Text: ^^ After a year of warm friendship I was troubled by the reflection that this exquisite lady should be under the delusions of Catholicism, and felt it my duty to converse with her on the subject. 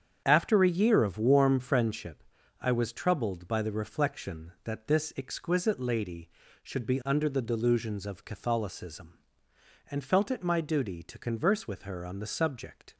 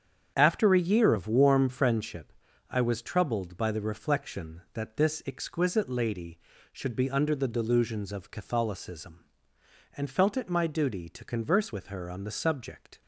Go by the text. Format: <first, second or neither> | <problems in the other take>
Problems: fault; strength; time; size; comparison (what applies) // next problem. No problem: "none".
neither | starts louder than the rest; strong; the same in both // pauses between "friendship" and "I"; the same in both